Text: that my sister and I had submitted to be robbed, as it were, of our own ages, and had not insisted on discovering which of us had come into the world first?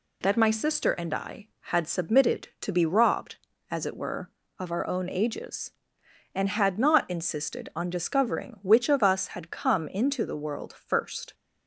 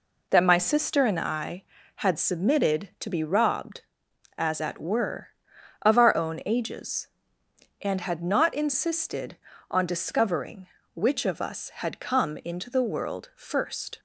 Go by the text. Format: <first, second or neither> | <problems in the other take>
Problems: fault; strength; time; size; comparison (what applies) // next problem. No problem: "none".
first | says "at" for "it"; at 4.5 s